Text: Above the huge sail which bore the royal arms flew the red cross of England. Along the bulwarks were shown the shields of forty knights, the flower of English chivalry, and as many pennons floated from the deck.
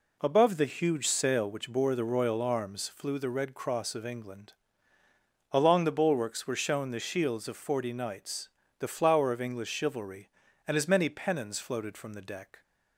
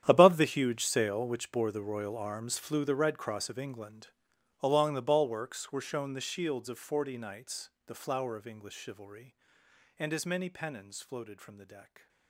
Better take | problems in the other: first | gets quieter; strong; throughout; 18 dB

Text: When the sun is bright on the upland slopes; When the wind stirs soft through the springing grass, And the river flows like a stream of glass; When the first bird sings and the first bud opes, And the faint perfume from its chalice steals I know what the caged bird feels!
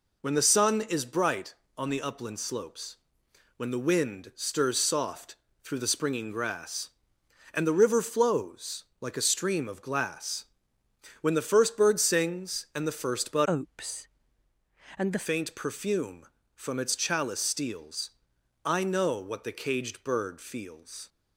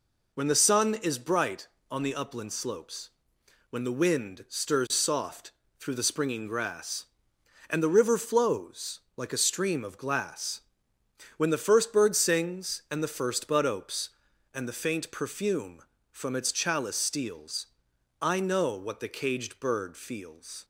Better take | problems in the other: second | pauses between "soft" and "through"; slight; at 5.3 s; 0.26 s long; slight in the second // pauses between "flows" and "like"; slight; at 8.8 s; 0.16 s long; slight in the second // changes voice from "opes" to "the"; from 13.4 to 15.2 s; 1.8 s long // pauses between "steals" and "I"; noticeable; at 18.1 s; 0.54 s long; noticeable in the second

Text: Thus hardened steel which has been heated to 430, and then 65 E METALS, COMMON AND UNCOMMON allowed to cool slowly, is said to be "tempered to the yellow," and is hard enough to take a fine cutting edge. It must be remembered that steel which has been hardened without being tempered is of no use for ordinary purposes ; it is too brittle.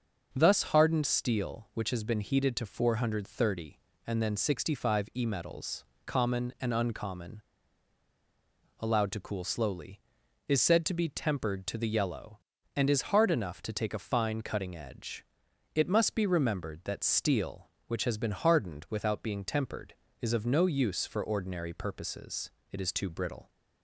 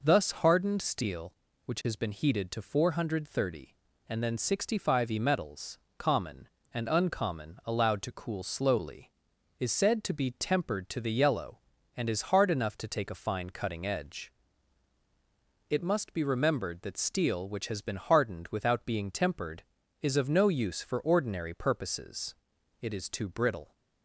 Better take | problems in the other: second | starts louder than the rest; until 1.3 s; 6.5 dB // pauses between "UNCOMMON" and "allowed"; strong; at 7.4 s; 1.3 s long

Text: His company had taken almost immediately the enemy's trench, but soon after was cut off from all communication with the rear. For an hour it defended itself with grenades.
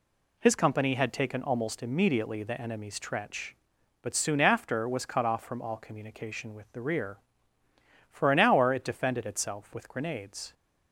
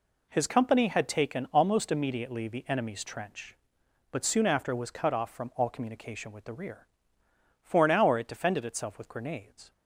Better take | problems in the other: neither | none

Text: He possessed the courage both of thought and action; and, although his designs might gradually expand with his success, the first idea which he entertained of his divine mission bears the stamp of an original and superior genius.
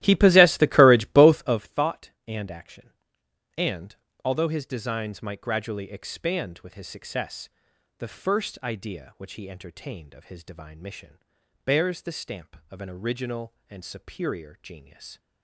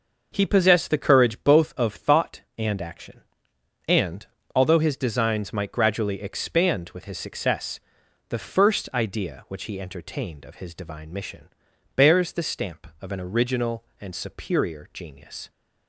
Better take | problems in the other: second | starts louder than the rest; strong; until 1.6 s; 14.5 dB // pauses between "mission" and "bears"; noticeable; at 11.1 s; 0.46 s long; noticeable in the second

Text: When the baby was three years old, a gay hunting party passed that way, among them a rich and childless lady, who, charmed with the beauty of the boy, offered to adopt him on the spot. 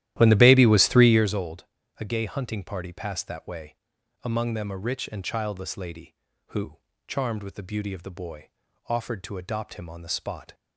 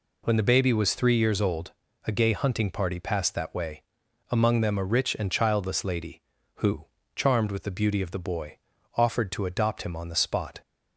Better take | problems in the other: second | starts louder than the rest; strong; until 1.5 s; 13.5 dB

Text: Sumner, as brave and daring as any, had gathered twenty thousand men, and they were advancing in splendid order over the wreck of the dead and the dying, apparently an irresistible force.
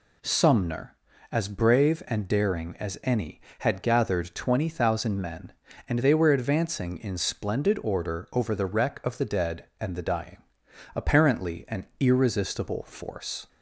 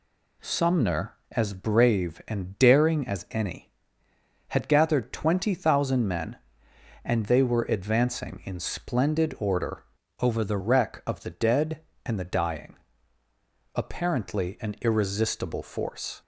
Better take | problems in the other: first | changes voice from "over" to "the"; from 10.2 to 10.5 s; 0.3 s long

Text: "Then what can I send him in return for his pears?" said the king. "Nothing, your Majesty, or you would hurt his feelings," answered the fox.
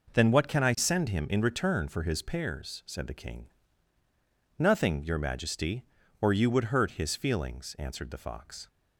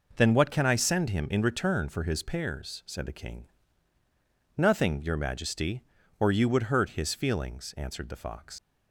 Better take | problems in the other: first | leaves "fox" unfinished; at 8.5 s; 70 ms

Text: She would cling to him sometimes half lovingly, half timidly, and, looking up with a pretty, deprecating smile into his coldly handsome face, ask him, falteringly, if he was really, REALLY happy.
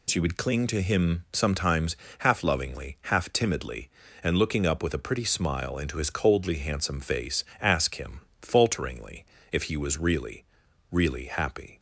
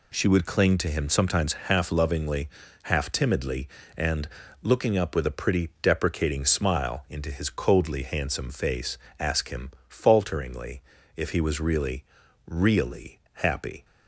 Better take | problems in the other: second | pauses between "sometimes" and "half"; slight; at 1.9 s; 0.24 s long // skips "deprecating"; at 5.2 s

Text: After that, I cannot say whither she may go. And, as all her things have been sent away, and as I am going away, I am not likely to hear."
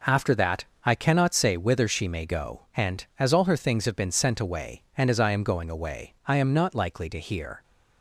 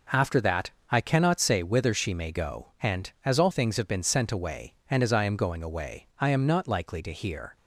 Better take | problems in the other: first | skips "her"; at 3.5 s

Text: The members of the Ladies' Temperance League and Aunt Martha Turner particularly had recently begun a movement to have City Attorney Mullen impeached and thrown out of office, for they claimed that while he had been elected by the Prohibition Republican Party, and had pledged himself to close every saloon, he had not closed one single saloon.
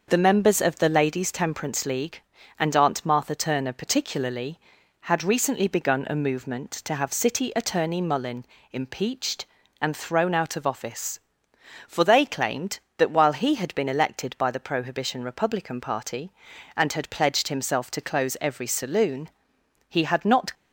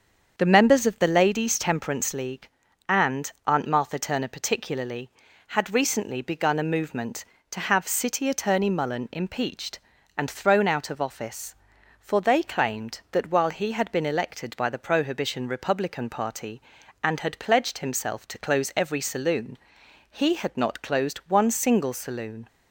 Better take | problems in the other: second | starts louder than the rest; until 1.0 s; 6.5 dB; strong in the second // pauses between "Mullen" and "impeached"; slight; at 8.4 s; 0.30 s long // stops before "closed one single saloon"; at 20.5 s

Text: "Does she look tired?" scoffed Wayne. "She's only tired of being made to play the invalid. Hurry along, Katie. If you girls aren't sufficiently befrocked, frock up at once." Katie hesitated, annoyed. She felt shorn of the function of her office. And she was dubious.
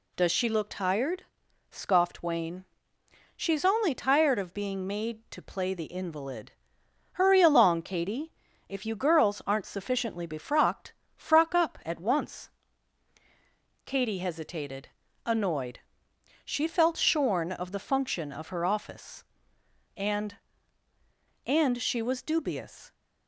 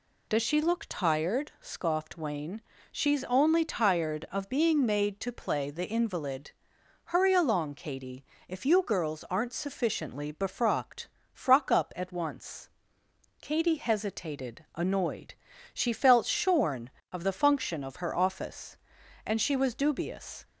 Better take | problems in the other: second | says "And" twice; at 21.4 s

